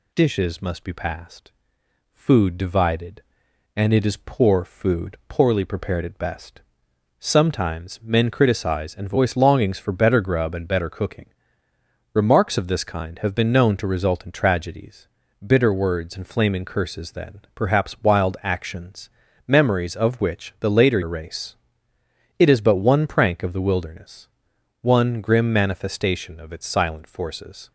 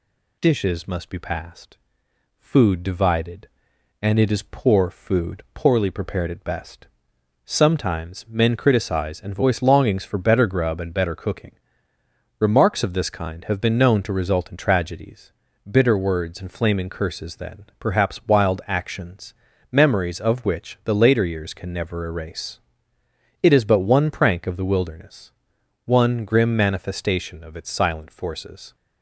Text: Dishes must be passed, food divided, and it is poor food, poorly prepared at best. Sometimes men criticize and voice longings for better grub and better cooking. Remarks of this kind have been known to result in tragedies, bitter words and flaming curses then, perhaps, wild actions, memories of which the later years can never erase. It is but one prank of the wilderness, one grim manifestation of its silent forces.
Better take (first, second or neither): second